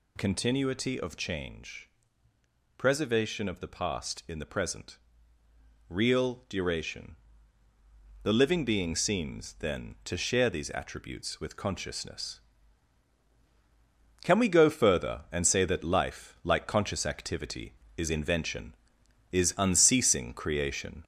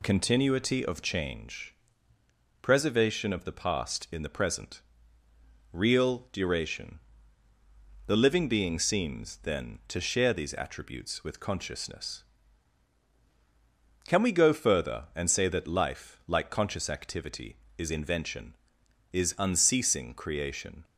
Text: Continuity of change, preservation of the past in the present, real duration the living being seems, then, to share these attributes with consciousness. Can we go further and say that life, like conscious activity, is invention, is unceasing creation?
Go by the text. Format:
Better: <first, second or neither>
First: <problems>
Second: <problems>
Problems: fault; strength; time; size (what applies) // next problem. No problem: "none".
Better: second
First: gets louder; noticeable; throughout; 4 dB // pauses between "duration" and "the"; at 7.1 s; 1.0 s long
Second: pauses between "duration" and "the"; at 7.0 s; 1.0 s long